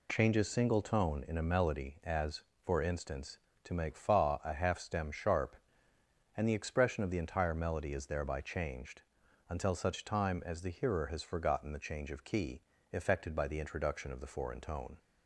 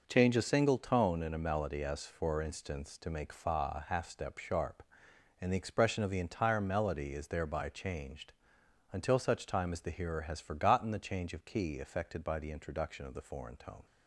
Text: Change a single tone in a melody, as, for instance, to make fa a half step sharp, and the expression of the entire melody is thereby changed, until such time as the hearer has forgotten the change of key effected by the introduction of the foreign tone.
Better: second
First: says "stem" for "step"; at 4.7 s // pauses between "key" and "effected"; slight; at 12.6 s; 0.30 s long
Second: none

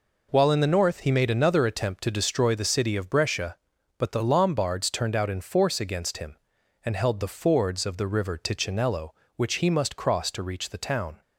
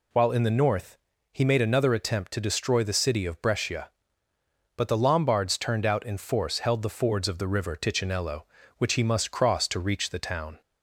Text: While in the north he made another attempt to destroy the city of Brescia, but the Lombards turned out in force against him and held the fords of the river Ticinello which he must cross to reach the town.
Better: first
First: none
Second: pauses between "north" and "he"; slight; at 0.9 s; 0.34 s long // skips "against him and"; at 6.5 s

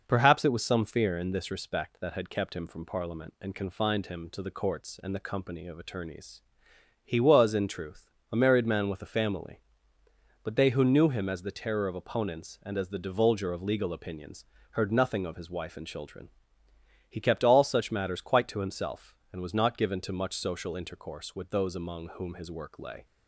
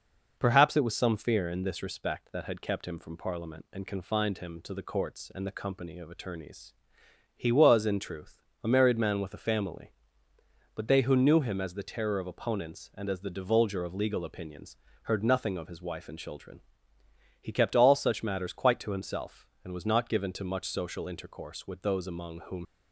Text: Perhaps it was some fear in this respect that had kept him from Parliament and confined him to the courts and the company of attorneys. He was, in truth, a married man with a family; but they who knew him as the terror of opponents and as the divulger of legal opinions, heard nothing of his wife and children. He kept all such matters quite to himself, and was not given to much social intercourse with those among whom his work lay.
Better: first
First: none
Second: stops before "his work lay"; at 22.6 s

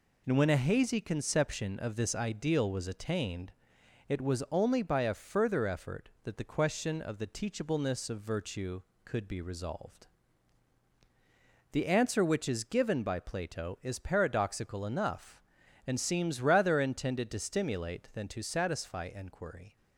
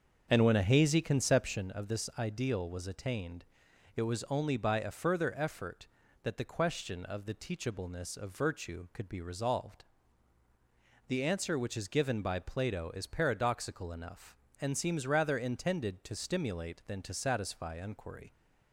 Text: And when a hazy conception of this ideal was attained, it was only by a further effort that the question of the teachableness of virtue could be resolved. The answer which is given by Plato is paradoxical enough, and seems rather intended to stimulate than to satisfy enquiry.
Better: first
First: none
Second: starts louder than the rest; until 1.7 s; 7 dB

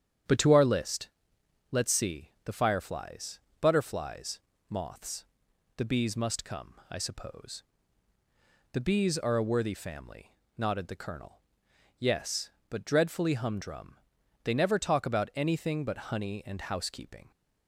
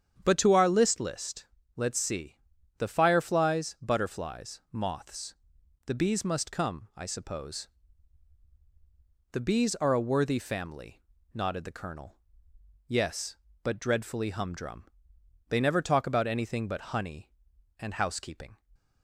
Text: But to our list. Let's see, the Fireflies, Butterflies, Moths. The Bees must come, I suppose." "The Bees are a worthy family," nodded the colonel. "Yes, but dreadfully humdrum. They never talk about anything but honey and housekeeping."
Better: first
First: starts louder than the rest; strong; until 1.8 s; 9 dB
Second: starts louder than the rest; strong; until 1.2 s; 8.5 dB // says "list" twice; at 0.9 s

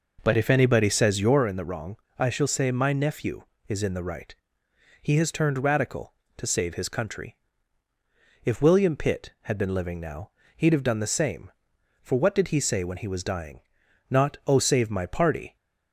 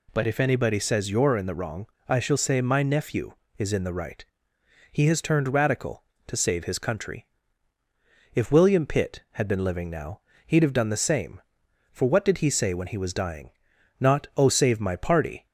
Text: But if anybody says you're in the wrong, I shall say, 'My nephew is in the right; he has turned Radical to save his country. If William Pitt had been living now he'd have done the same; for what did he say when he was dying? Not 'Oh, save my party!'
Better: second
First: starts louder than the rest; noticeable; until 1.5 s; 5 dB // pauses between "now" and "he'd"; slight; at 10.3 s; 0.26 s long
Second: pauses between "now" and "he'd"; slight; at 10.2 s; 0.26 s long

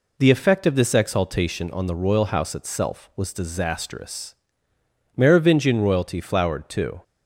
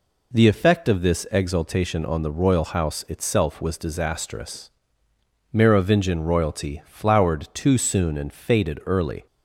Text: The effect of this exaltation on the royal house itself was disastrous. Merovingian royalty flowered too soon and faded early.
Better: second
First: stops before "soon and faded early"; at 7.0 s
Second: none

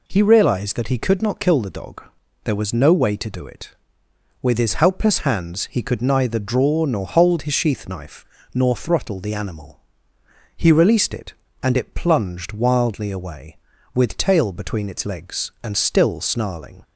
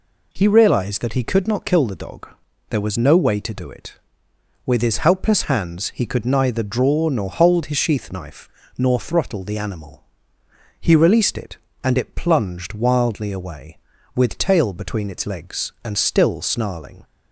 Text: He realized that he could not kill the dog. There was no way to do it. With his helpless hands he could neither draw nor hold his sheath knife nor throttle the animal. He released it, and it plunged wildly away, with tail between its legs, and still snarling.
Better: neither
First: pauses between "knife" and "nor"; slight; at 8.2 s; 0.30 s long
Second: pauses between "knife" and "nor"; slight; at 8.4 s; 0.30 s long

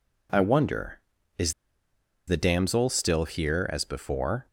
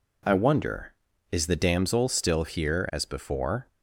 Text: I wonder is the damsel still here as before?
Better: second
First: pauses between "is" and "the"; noticeable; at 1.5 s; 0.75 s long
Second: none

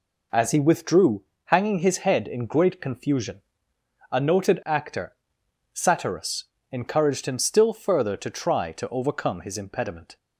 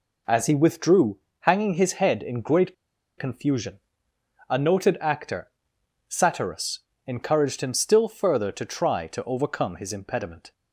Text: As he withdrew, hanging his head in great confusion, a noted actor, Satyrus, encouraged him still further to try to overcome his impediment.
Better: first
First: none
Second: pauses between "great" and "confusion"; at 2.7 s; 0.43 s long

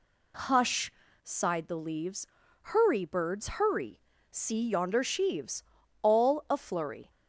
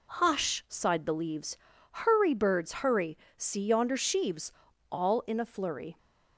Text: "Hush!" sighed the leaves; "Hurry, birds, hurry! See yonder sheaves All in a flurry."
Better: second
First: pauses between "sheaves" and "All"; at 5.6 s; 0.38 s long // skips "in"; at 6.4 s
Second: pauses between "sheaves" and "All"; at 4.5 s; 0.40 s long

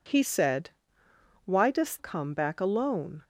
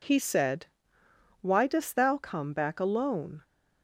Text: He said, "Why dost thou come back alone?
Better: second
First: skips "thou"; at 1.9 s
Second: none

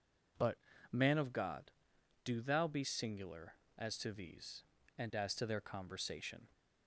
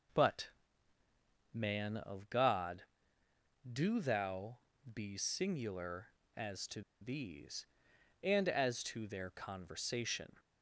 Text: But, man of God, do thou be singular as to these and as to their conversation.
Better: first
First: none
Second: pauses between "thou" and "be"; slight; at 4.5 s; 0.34 s long // pauses between "to" and "these"; slight; at 6.8 s; 0.20 s long

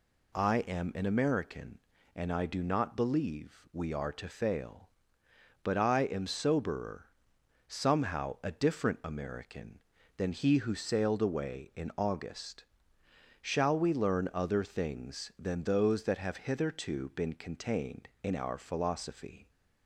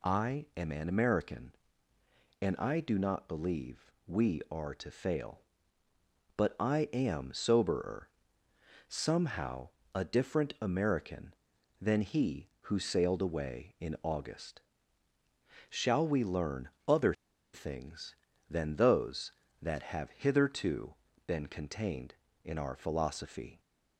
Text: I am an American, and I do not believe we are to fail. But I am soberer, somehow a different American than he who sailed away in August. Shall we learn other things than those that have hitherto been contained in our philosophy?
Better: first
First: none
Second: pauses between "believe" and "we"; slight; at 3.9 s; 0.16 s long // pauses between "somehow" and "a"; slight; at 9.6 s; 0.26 s long // pauses between "learn" and "other"; slight; at 16.6 s; 0.18 s long // pauses between "other" and "things"; at 17.1 s; 0.40 s long // pauses between "hitherto" and "been"; slight; at 20.9 s; 0.32 s long

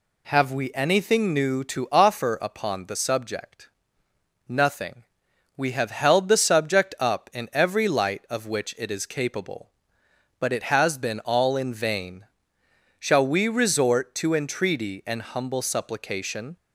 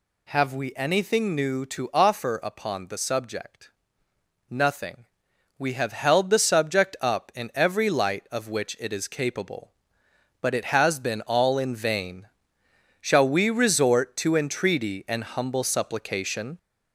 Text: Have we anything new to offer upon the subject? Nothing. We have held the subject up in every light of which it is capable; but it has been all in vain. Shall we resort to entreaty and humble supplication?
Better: first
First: none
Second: gets louder; slight; throughout; 2.5 dB

